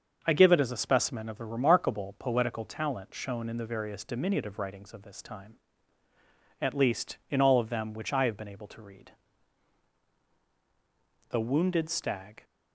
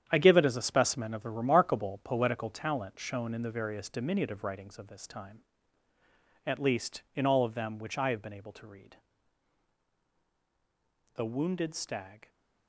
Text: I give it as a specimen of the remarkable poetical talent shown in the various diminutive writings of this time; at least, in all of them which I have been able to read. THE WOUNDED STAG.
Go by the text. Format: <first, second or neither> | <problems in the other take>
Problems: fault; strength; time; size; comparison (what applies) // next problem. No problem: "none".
first | gets quieter; strong; throughout; 10.5 dB // starts louder than the rest; strong; until 1.0 s; 9 dB; also in the first